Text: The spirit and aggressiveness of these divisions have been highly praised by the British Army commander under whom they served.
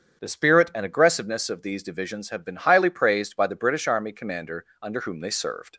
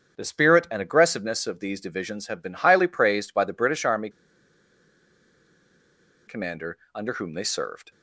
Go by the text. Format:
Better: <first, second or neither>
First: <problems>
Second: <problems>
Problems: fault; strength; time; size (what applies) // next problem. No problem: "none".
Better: first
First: starts louder than the rest; strong; until 1.2 s; 7.5 dB // pauses between "commander" and "under"; slight; at 4.6 s; 0.16 s long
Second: starts louder than the rest; strong; until 1.2 s; 7.5 dB // pauses between "Army" and "commander"; strong; at 4.0 s; 2.1 s long // pauses between "commander" and "under"; slight; at 6.7 s; 0.16 s long